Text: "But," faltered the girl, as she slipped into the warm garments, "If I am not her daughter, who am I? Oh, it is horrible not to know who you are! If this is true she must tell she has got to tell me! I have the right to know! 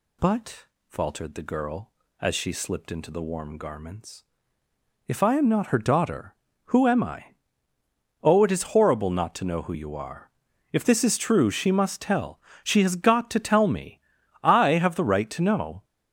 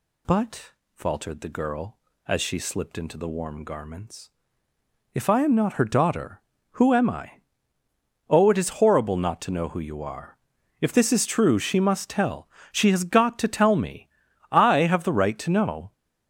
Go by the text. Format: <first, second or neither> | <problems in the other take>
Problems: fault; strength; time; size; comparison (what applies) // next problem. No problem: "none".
neither | pauses between "tell" and "she"; slight; the same in both